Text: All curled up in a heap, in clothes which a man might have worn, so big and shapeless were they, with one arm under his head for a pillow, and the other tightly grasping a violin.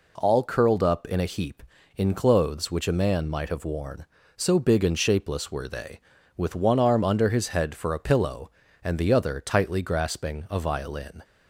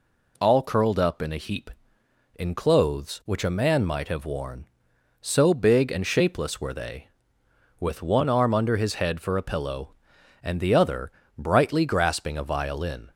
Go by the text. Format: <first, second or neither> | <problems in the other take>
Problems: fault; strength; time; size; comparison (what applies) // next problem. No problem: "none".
first | says "brightly" for "tightly"; at 11.3 s